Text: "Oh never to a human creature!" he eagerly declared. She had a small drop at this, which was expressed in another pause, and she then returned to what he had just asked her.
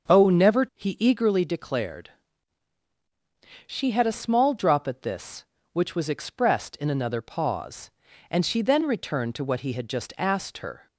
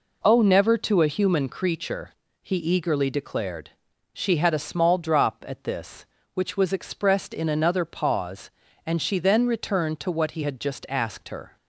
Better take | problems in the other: second | starts louder than the rest; until 1.2 s; 7 dB // skips "to a human creature"; at 0.6 s

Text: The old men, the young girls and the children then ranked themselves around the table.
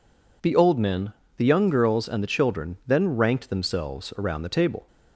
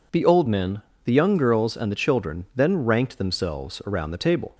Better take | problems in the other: neither | none

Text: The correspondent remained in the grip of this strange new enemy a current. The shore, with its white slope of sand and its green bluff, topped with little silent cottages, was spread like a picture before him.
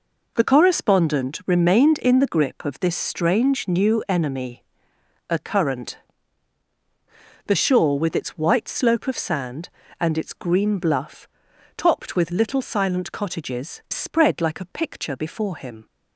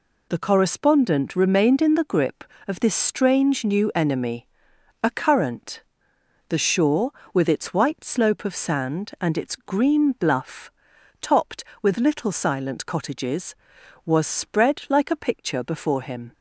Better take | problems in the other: second | pauses between "enemy" and "a"; noticeable; at 4.6 s; 0.66 s long; noticeable in the second // skips "was"; at 13.8 s

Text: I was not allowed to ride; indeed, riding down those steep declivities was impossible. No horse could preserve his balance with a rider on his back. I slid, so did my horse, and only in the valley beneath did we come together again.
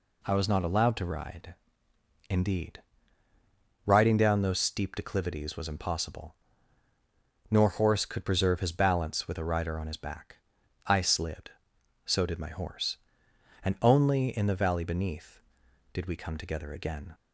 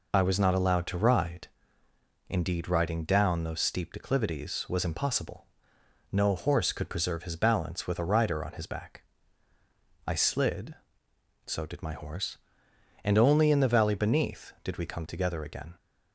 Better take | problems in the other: second | says "Nor" for "No"; at 7.4 s

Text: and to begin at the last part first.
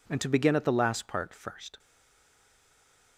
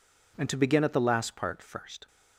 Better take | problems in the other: second | stays silent after the last word; noticeable; from 1.7 s on; 1.4 s long

